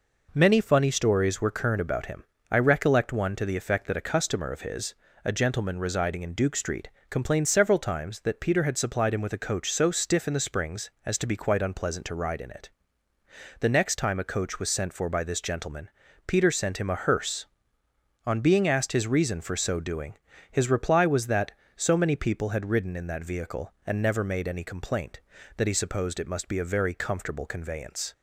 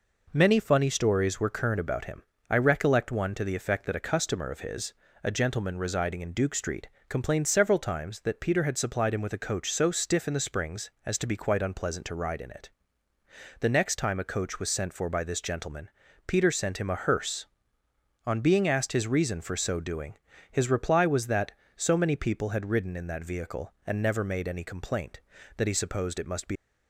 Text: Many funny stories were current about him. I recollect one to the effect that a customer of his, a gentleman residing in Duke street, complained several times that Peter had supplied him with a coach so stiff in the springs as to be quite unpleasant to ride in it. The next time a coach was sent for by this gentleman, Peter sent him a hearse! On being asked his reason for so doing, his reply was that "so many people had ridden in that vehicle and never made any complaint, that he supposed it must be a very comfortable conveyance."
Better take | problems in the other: first | stops before "a very comfortable conveyance"; at 26.5 s

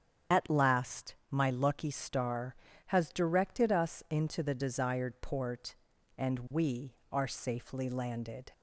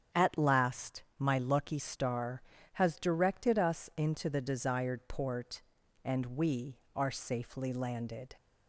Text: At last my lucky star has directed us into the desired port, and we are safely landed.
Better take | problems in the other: second | loses the start of "At"; at 0.3 s; 45 ms // starts louder than the rest; strong; until 1.4 s; 8.5 dB; strong in the second // pauses between "last" and "my"; slight; at 1.1 s; 0.16 s long; slight in the second

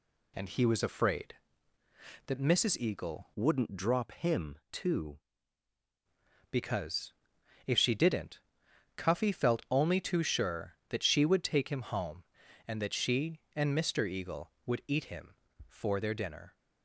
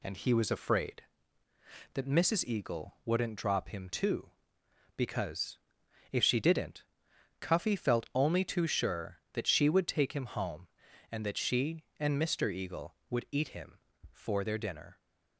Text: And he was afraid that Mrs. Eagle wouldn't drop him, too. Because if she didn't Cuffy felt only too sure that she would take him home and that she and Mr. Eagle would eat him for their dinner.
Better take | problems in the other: second | changes voice from "wouldn't" to "too"; from 3.3 to 5.1 s; 1.8 s long // pauses between "Because" and "if"; noticeable; at 7.1 s; 0.54 s long; noticeable in the second // pauses between "didn't" and "Cuffy"; noticeable; at 8.3 s; 0.56 s long; noticeable in the second

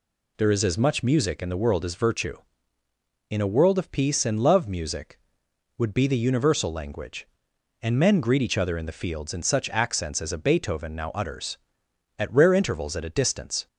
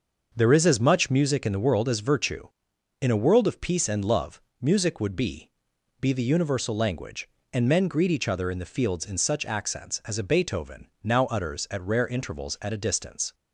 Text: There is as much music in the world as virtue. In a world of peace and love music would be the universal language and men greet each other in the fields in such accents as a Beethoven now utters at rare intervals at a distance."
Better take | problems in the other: first | starts louder than the rest; noticeable; until 1.3 s; 6 dB // pauses between "love" and "music"; slight; at 4.3 s; 0.22 s long // says "be" twice; at 5.9 s // pauses between "Beethoven" and "now"; slight; at 10.8 s; 0.16 s long

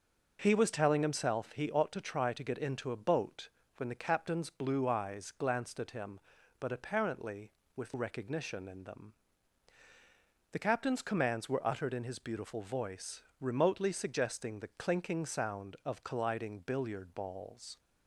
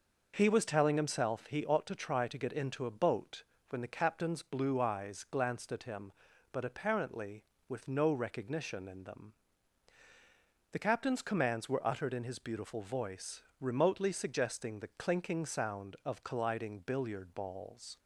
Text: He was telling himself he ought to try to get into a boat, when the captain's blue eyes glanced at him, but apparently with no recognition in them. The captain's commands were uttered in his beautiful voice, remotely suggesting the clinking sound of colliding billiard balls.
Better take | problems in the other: second | skips "no"; at 7.9 s

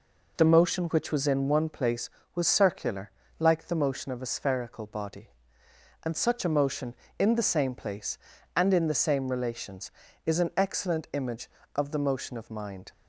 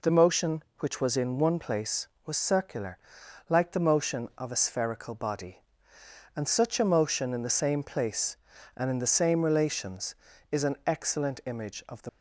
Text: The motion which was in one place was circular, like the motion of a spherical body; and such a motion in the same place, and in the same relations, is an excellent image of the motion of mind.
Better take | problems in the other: first | stops before "motion of mind"; at 12.0 s

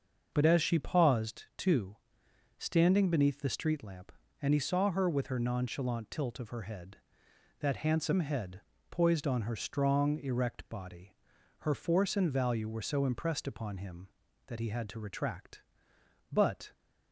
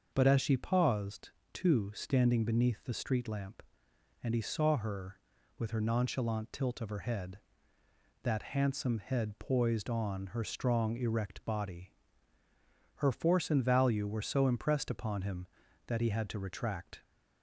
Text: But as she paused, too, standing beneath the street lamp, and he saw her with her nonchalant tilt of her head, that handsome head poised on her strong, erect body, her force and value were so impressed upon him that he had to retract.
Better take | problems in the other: second | starts louder than the rest; until 1.3 s; 6.5 dB; also in the second // pauses between "head" and "poised"; slight; at 8.6 s; 0.30 s long // goes on to say "But"; slight; from 16.3 s on; 0.40 s long

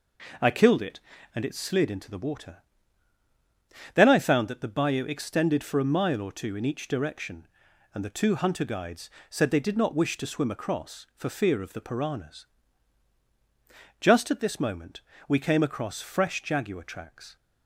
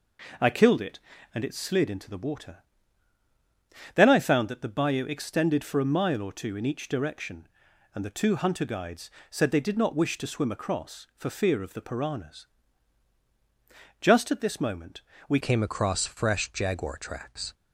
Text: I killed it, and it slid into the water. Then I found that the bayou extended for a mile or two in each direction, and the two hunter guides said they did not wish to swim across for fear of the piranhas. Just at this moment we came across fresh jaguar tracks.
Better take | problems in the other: first | pauses between "guides" and "said"; slight; at 9.1 s; 0.20 s long; slight in the first // pauses between "moment" and "we"; slight; at 15.0 s; 0.26 s long; slight in the first // changes voice at "came"; from 15.4 s on; 2.1 s long

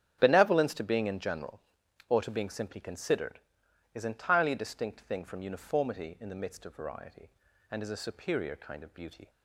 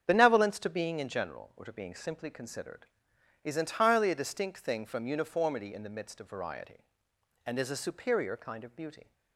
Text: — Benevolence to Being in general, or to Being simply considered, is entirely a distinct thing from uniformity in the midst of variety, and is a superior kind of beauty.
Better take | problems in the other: neither | starts louder than the rest; strong; the same in both

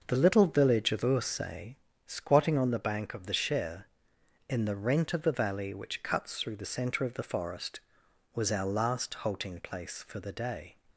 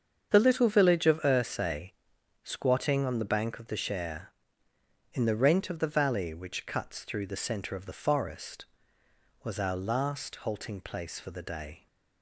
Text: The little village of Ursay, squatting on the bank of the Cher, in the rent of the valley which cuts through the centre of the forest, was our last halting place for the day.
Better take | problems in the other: neither | starts louder than the rest; the same in both

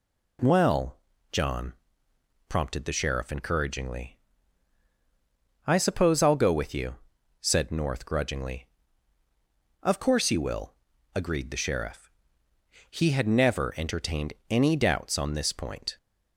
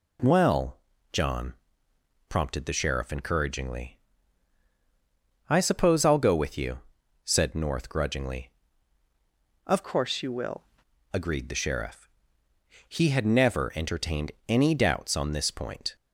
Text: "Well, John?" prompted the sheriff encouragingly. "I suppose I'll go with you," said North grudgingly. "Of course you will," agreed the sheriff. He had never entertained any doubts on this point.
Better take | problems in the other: first | changes voice from "course" to "will"; from 9.8 to 10.6 s; 0.8 s long // pauses between "entertained" and "any"; slight; at 14.3 s; 0.16 s long; slight in the first

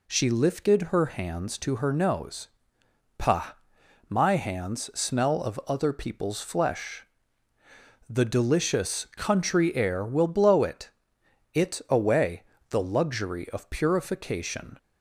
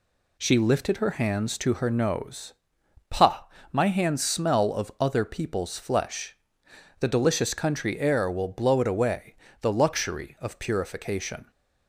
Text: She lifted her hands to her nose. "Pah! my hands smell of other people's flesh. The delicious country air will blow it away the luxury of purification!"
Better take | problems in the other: second | says "it" twice; at 11.5 s // pauses between "away" and "the"; slight; at 12.4 s; 0.26 s long; slight in the second

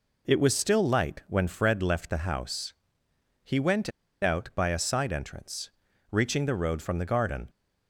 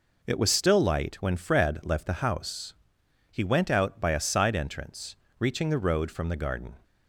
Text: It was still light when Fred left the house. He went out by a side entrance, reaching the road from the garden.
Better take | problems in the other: second | pauses between "went" and "out"; slight; at 3.8 s; 0.33 s long

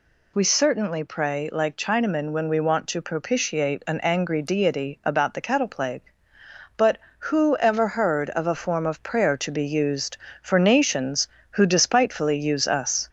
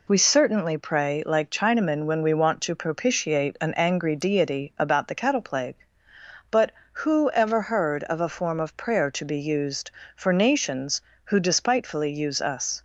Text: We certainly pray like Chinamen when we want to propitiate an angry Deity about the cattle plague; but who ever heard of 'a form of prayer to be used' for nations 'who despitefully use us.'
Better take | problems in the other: second | gets louder; slight; throughout; 2.5 dB

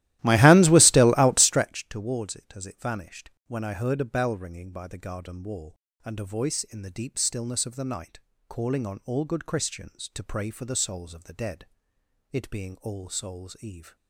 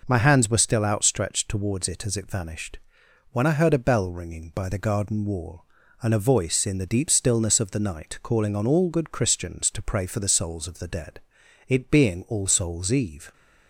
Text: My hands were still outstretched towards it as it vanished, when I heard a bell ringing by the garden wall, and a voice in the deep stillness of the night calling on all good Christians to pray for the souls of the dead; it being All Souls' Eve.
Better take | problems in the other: second | starts louder than the rest; strong; until 1.7 s; 15.5 dB // pauses between "night" and "calling"; slight; at 8.1 s; 0.30 s long

